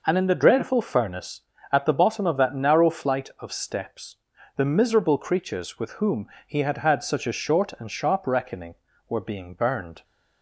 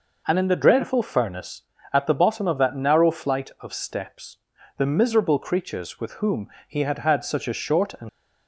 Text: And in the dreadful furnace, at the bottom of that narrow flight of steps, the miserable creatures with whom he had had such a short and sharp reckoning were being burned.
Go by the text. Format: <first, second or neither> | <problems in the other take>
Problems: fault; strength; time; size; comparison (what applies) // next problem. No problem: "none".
first | pauses between "whom" and "he"; slight; at 6.4 s; 0.20 s long; slight in the first // stops before "sharp reckoning were being burned"; at 8.0 s